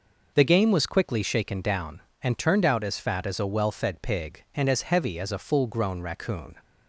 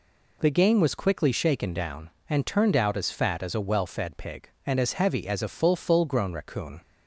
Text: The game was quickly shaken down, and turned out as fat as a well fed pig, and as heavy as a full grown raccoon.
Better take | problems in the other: first | says "full" twice; at 5.7 s

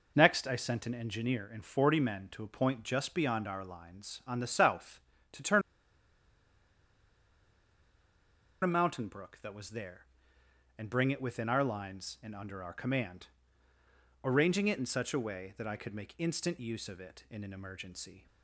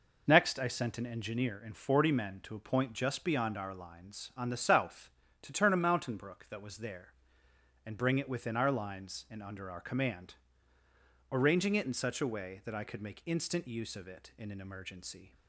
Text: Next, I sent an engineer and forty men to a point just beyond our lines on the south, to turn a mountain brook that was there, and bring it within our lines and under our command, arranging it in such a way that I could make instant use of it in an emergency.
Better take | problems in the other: second | pauses between "turn" and "a"; strong; at 5.6 s; 3.0 s long

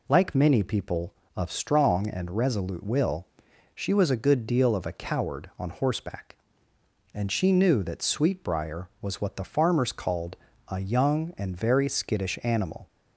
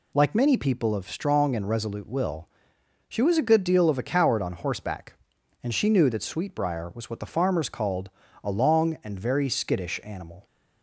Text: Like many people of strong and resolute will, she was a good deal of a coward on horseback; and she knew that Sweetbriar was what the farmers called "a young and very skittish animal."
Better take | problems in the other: first | pauses between "called" and "a"; slight; at 8.1 s; 0.32 s long; slight in the first // says "long" for "young"; at 8.5 s

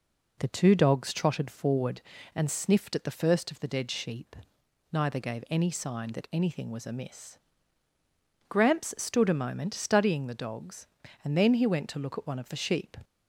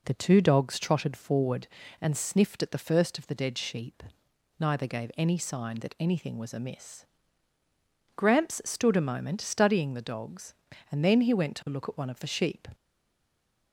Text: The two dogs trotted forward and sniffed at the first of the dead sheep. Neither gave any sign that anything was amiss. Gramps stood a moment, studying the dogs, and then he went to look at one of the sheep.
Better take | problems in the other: first | stays silent after the last word; from 12.7 s on; 1.0 s long

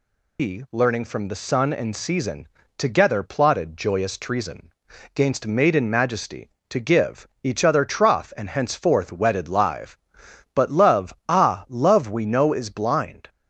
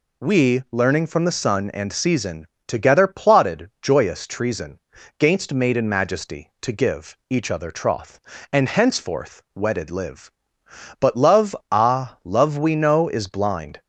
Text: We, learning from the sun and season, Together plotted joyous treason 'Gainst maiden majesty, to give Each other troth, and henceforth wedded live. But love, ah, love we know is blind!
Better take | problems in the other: second | loses the start of "We"; at 0.3 s; 125 ms // pauses between "treason" and "Gainst"; at 4.7 s; 0.44 s long; also in the second // pauses between "give" and "Each"; slight; at 7.2 s; 0.16 s long

